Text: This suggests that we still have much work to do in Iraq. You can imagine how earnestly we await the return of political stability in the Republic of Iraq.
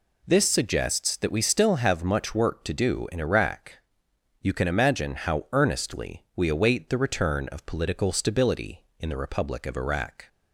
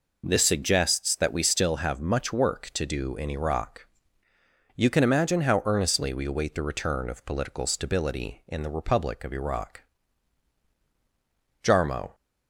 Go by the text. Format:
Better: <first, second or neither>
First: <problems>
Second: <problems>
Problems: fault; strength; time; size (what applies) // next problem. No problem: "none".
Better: first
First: none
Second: goes on to say "JARMO"; from 11.6 s on; 0.52 s long